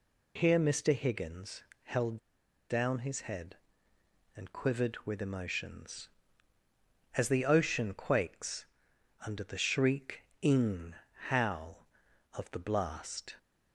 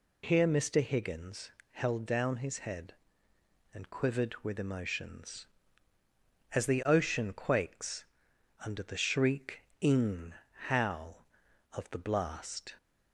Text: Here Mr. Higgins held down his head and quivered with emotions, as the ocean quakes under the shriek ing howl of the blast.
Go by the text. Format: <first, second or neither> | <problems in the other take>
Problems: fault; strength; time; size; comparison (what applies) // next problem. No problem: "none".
second | pauses between "Higgins" and "held"; slight; at 1.6 s; 0.22 s long; slight in the second // pauses between "held" and "down"; noticeable; at 2.1 s; 0.51 s long // pauses between "quakes" and "under"; noticeable; at 8.6 s; 0.52 s long; noticeable in the second // pauses between "shriek" and "ing"; slight; at 10.2 s; 0.18 s long; slight in the second // pauses between "ing" and "howl"; slight; at 10.9 s; 0.32 s long; slight in the second